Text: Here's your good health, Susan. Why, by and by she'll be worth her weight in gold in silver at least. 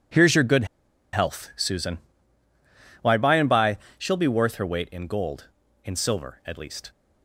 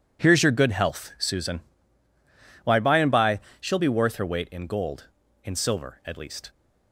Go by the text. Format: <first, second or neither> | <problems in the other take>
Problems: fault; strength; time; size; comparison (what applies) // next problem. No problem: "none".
second | pauses between "good" and "health"; noticeable; at 0.6 s; 0.48 s long // pauses between "by" and "she'll"; slight; at 3.7 s; 0.18 s long; slight in the second